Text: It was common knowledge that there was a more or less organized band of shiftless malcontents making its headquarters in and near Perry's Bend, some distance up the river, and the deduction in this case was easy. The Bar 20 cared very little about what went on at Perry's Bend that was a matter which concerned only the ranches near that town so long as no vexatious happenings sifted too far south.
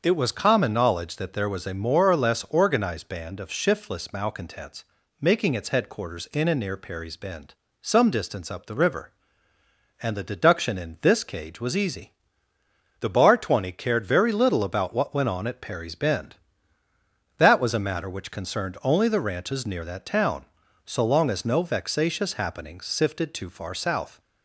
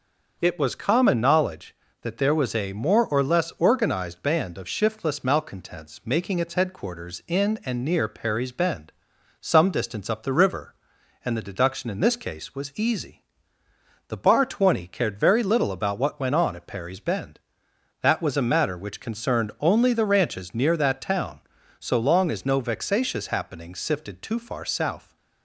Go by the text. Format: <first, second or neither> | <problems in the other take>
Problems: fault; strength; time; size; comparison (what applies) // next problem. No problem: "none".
second | starts louder than the rest; until 1.0 s; 7 dB; also in the second // pauses between "malcontents" and "making"; slight; at 4.8 s; 0.36 s long // says "cage" for "case"; at 11.2 s